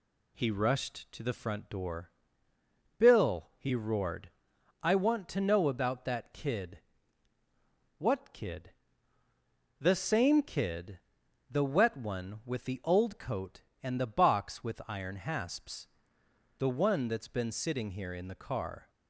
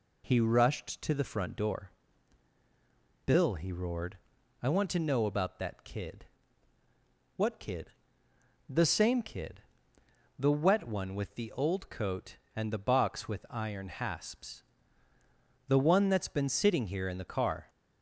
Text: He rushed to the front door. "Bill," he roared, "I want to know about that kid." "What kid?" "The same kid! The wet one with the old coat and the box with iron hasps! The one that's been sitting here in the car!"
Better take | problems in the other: neither | none

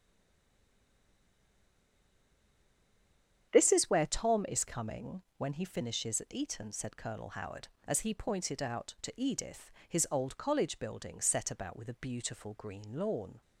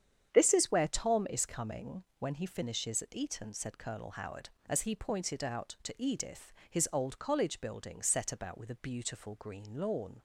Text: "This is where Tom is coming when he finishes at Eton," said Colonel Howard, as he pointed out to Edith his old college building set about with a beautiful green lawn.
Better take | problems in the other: second | stays silent before the first word; strong; until 3.5 s; 3.5 s long // starts louder than the rest; strong; until 4.5 s; 8.5 dB; strong in the second // pauses between "coming" and "when"; slight; at 5.2 s; 0.16 s long; slight in the second // pauses between "Edith" and "his"; slight; at 9.7 s; 0.18 s long; slight in the second

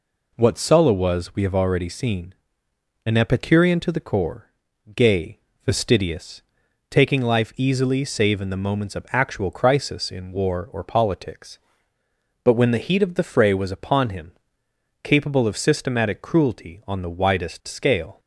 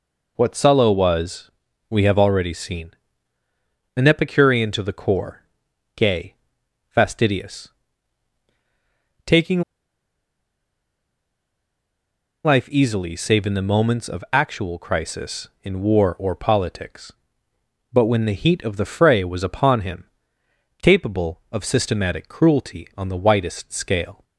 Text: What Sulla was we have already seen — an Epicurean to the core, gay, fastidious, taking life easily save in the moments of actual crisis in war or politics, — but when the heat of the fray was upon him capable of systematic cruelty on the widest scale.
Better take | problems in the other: first | pauses between "was" and "we"; at 1.5 s; 0.38 s long // pauses between "taking" and "life"; strong; at 9.6 s; 2.8 s long // pauses between "him" and "capable"; noticeable; at 20.0 s; 0.78 s long; noticeable in the first

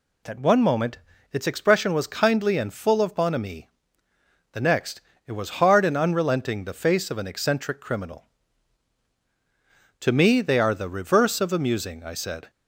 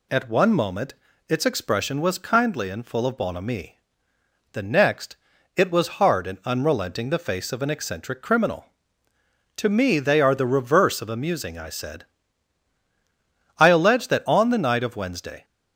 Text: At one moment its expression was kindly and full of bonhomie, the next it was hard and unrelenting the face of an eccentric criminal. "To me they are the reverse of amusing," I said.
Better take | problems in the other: first | pauses between "moment" and "its"; slight; at 0.9 s; 0.34 s long; slight in the first // pauses between "next" and "it"; at 5.1 s; 0.38 s long; slight in the first // goes on to say "I allege that on the night of Wednesday"; strong; from 13.5 s on; 1.8 s long

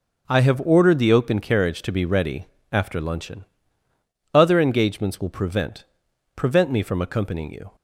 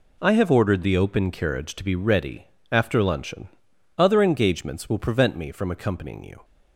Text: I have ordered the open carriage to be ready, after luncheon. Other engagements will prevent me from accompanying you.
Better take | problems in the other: second | says "prevent" twice; at 6.3 s

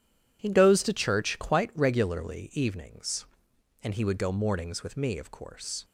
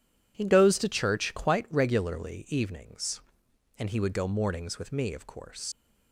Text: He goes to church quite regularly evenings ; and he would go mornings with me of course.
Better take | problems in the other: first | leaves "course" unfinished; at 5.7 s; 80 ms

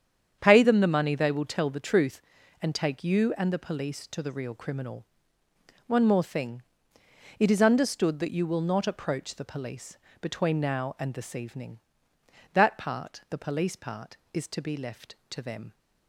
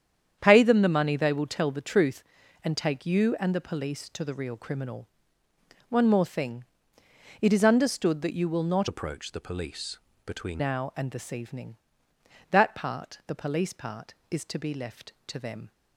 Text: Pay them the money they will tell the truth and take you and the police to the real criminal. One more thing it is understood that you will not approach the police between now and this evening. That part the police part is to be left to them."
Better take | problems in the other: first | starts louder than the rest; strong; until 1.4 s; 8.5 dB; strong in the first // pauses between "thing" and "it"; noticeable; at 6.6 s; 0.76 s long; noticeable in the first // changes voice from "approach" to "between"; from 8.8 to 10.6 s; 1.8 s long // pauses between "police" and "between"; slight; at 9.9 s; 0.28 s long; slight in the first

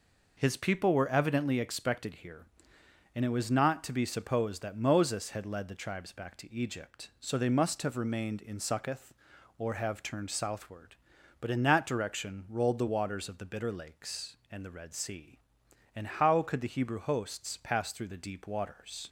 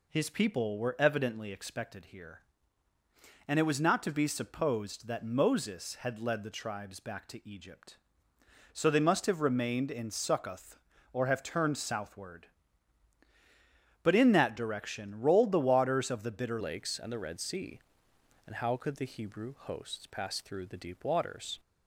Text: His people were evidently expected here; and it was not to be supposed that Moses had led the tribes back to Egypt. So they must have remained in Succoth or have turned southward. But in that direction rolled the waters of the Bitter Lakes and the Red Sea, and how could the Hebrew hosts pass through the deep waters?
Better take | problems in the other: first | changes voice at "Lakes"; from 16.6 s on; 4.9 s long

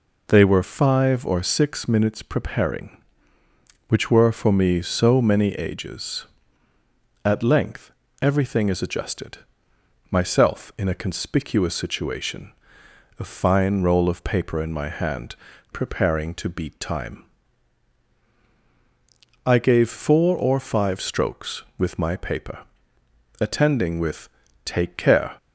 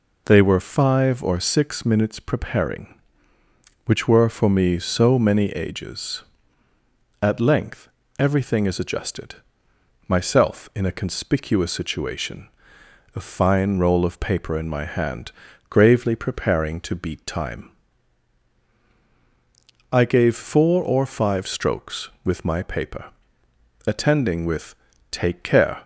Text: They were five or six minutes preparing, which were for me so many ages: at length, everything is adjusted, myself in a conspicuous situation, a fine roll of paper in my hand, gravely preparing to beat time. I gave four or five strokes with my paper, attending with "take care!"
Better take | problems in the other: second | skips "gravely"; at 15.5 s // pauses between "with" and "take"; at 24.2 s; 0.38 s long; also in the second

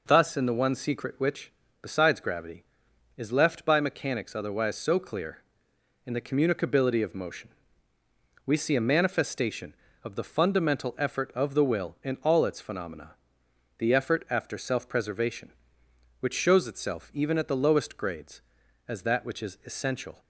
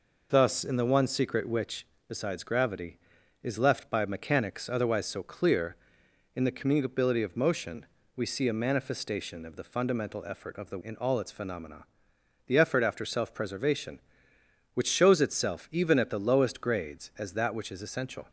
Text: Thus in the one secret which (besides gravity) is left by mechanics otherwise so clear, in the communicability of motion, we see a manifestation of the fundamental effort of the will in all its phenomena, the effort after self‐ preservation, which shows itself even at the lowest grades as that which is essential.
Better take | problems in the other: first | skips "will"; at 10.8 s

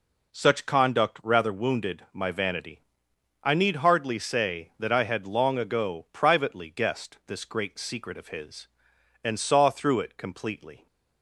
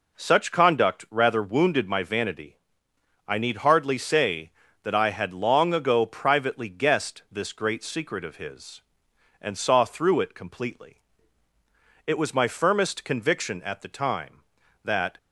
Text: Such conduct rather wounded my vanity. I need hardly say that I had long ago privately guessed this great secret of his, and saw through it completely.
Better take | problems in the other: first | goes on to say "It was my firmest conviction at the time that"; strong; from 12.0 s on; 3.1 s long

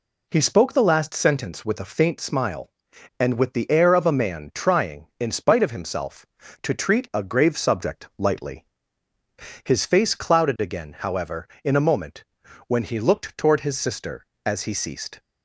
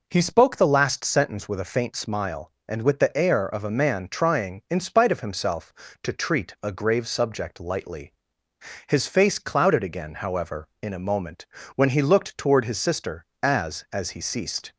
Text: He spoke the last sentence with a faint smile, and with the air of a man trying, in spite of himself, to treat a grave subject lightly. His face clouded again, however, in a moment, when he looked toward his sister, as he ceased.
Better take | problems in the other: first | says "as" twice; at 13.9 s

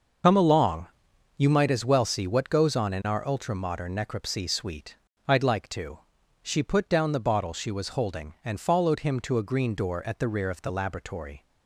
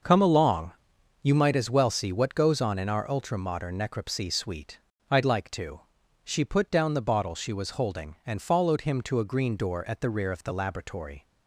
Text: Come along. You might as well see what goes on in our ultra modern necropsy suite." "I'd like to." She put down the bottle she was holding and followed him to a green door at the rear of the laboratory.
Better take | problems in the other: second | loses the start of "Come"; at 0.2 s; 60 ms // starts louder than the rest; until 1.7 s; 6 dB; also in the second

